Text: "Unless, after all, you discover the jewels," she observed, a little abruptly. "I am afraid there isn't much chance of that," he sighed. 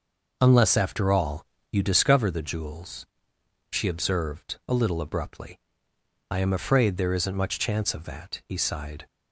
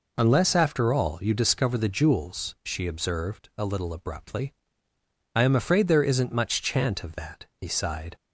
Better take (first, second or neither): first